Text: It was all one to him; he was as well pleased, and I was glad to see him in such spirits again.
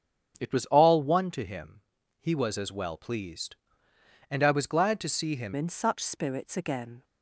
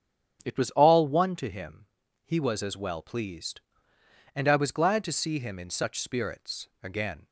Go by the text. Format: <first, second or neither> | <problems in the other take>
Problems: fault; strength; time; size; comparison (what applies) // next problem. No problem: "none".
second | starts louder than the rest; strong; until 1.4 s; 8 dB; strong in the second // changes voice at "in"; from 5.5 s on; 1.5 s long